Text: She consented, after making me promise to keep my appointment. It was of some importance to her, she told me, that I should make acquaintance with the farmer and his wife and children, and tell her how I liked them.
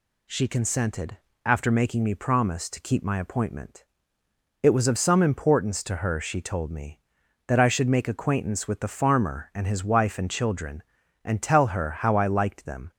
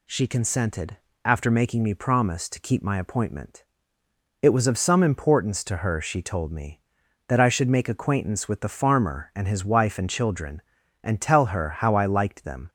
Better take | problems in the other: neither | none

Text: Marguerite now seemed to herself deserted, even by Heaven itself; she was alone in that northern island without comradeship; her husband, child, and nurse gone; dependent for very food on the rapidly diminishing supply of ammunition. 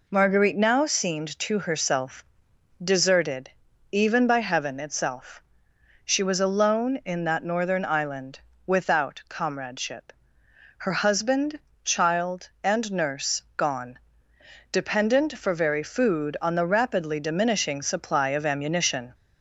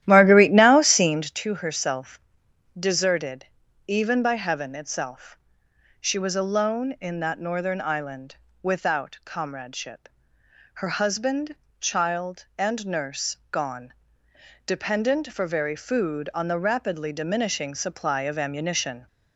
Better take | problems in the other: first | starts louder than the rest; strong; until 1.4 s; 12.5 dB // pauses between "herself" and "deserted"; noticeable; at 2.1 s; 0.58 s long; noticeable in the first // pauses between "island" and "without"; slight; at 8.3 s; 0.28 s long; slight in the first

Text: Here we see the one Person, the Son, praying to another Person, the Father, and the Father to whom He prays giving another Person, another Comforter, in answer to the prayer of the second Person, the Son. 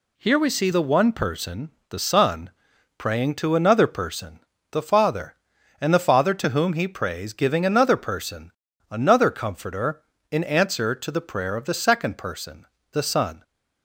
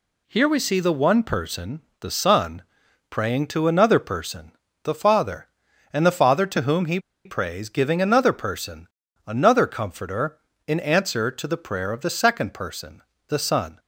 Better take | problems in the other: first | pauses between "He" and "prays"; slight; at 6.9 s; 0.26 s long

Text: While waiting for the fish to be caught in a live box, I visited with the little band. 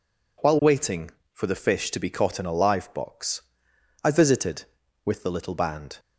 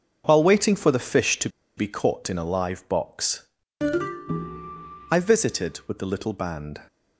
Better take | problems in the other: first | pauses between "to" and "be"; slight; at 1.4 s; 0.27 s long

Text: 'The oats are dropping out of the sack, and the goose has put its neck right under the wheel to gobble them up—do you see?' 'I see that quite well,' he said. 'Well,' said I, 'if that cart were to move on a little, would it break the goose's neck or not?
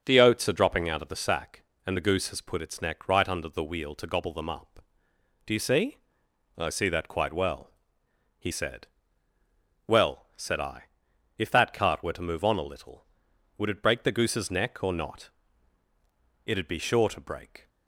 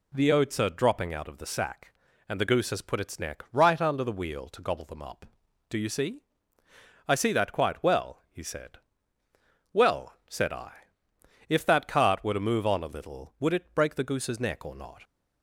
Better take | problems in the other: second | goes on to say "It'd be sure to break"; noticeable; from 16.4 s on; 1.2 s long

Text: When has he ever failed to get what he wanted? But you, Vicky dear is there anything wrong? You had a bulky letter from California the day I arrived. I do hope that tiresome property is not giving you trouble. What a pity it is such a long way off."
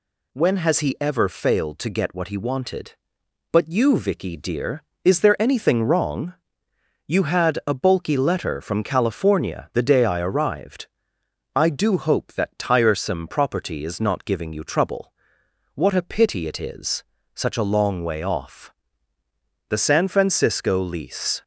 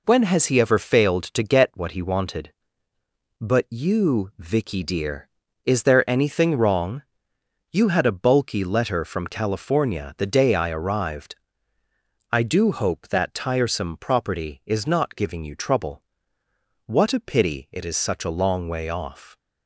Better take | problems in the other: second | pauses between "is" and "such"; slight; at 17.0 s; 0.30 s long // goes on to say "The San Francisco lease"; strong; from 19.6 s on; 1.7 s long

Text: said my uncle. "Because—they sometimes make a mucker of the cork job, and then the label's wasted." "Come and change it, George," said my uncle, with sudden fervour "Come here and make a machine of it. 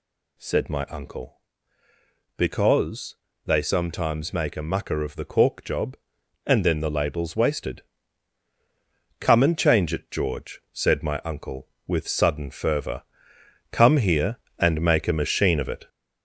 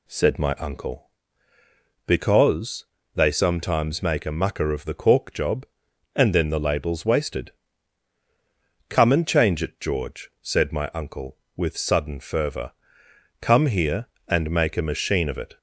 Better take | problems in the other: second | gets louder; noticeable; throughout; 5.5 dB // pauses between "fervour" and "Come"; noticeable; at 13.0 s; 0.70 s long; noticeable in the second

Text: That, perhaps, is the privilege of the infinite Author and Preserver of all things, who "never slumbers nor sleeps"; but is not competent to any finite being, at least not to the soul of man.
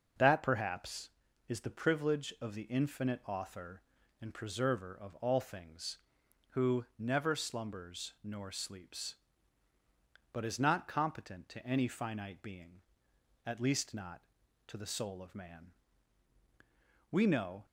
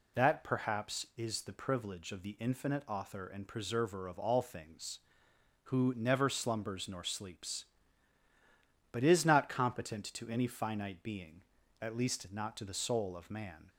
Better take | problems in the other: second | starts louder than the rest; until 1.5 s; 6.5 dB // goes on to say "We know"; from 17.1 s on; 0.54 s long

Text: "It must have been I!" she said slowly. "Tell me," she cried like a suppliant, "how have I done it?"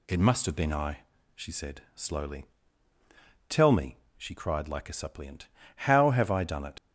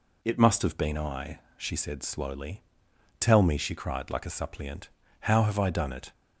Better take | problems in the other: second | leaves "it" unfinished; at 6.7 s; 75 ms

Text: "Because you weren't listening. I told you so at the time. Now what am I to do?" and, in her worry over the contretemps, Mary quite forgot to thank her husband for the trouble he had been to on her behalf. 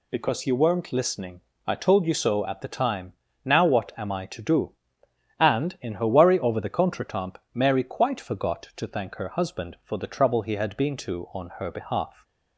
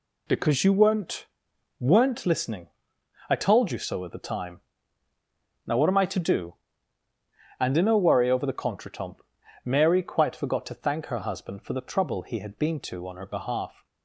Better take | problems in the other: first | says "weren't" twice; at 1.7 s

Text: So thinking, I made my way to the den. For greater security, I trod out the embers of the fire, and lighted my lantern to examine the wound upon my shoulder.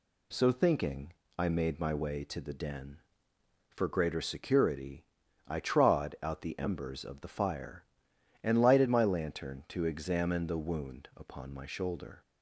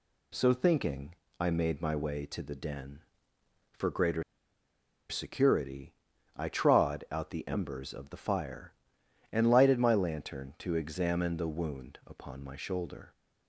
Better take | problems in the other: first | pauses between "greater" and "security"; noticeable; at 4.2 s; 0.86 s long

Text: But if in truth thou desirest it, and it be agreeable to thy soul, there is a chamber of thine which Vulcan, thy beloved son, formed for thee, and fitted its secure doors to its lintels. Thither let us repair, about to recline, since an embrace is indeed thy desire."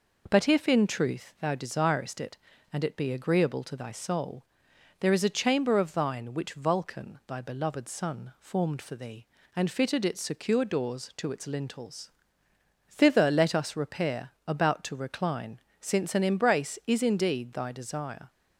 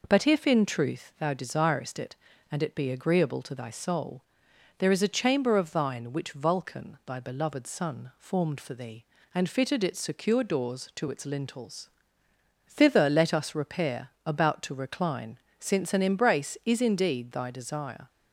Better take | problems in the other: neither | none

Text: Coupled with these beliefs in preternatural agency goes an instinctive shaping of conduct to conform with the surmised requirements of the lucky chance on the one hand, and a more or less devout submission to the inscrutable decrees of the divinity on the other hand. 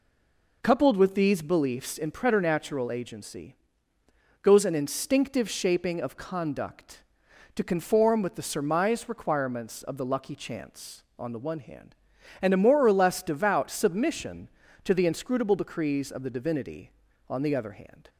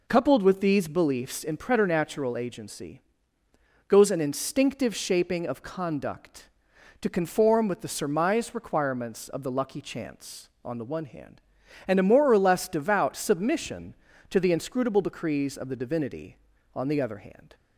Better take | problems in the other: second | stays silent before the first word; slight; until 0.6 s; 0.6 s long // pauses between "agency" and "goes"; noticeable; at 3.5 s; 0.88 s long; noticeable in the second

